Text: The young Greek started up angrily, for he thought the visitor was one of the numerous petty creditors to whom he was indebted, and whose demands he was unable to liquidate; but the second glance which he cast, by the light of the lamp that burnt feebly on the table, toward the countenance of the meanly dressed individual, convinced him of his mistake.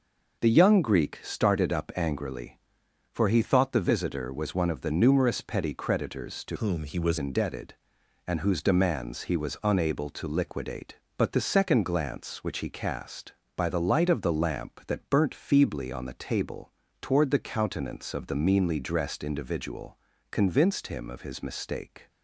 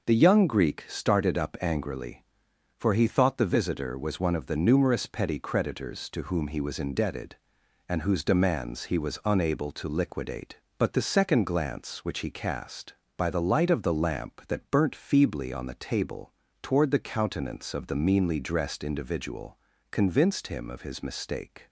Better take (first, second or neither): second